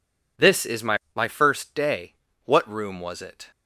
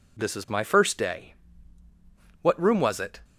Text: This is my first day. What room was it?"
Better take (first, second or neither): second